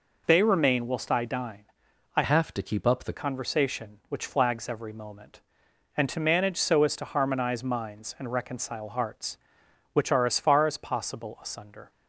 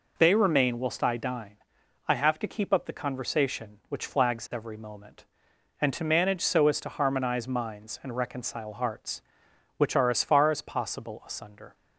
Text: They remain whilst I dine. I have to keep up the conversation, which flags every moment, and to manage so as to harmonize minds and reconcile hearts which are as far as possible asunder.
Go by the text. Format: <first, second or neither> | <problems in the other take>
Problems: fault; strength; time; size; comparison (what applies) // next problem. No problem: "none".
second | changes voice from "have" to "the"; from 2.2 to 3.1 s; 0.9 s long